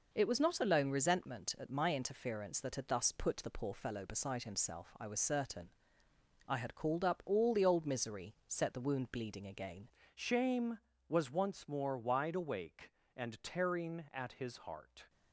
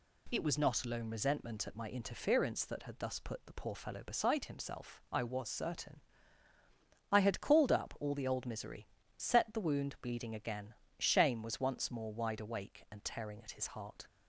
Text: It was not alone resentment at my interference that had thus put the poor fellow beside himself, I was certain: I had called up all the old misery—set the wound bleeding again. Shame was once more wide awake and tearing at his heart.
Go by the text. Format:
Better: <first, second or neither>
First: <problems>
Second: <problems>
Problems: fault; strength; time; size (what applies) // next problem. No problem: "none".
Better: second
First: changes voice at "Shame"; from 10.1 s on; 4.9 s long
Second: none